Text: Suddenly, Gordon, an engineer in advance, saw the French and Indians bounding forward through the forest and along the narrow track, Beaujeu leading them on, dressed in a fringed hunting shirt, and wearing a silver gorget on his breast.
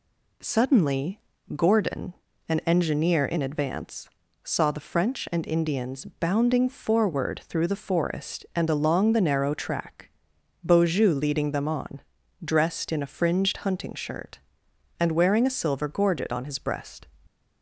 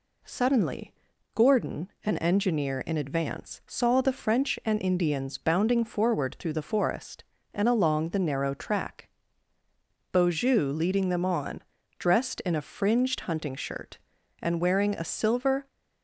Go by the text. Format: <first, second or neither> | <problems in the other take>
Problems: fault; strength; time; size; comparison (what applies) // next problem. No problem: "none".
first | stops before "gorget on his breast"; at 15.6 s